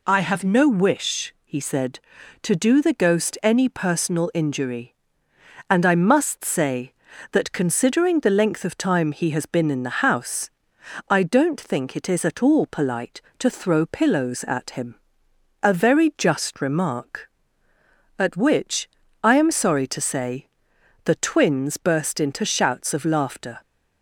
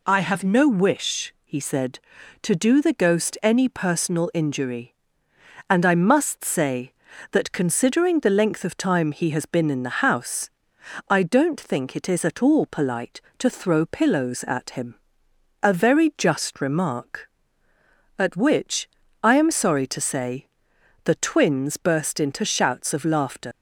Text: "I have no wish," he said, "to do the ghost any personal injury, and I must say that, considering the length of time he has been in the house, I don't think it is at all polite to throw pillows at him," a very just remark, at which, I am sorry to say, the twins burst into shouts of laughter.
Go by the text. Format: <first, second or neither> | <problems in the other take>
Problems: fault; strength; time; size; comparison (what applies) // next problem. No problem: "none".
first | leaves "laughter" unfinished; at 23.5 s; 90 ms